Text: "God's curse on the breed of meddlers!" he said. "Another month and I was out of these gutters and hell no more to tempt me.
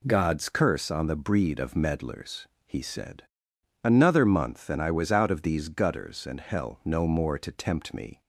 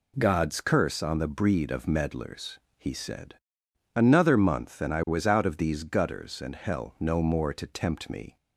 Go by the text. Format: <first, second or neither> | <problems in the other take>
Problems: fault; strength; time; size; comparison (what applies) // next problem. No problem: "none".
neither | none